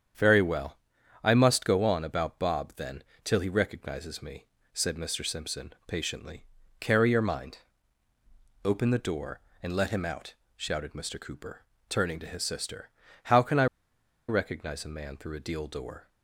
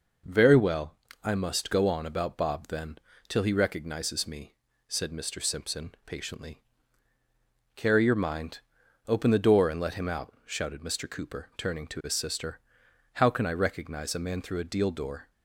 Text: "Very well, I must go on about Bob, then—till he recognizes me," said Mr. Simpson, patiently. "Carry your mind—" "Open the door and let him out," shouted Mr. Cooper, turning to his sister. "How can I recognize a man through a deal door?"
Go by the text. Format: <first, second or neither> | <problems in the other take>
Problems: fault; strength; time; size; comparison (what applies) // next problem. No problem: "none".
second | starts louder than the rest; strong; until 1.6 s; 8 dB // pauses between "I" and "recognize"; noticeable; at 13.6 s; 0.62 s long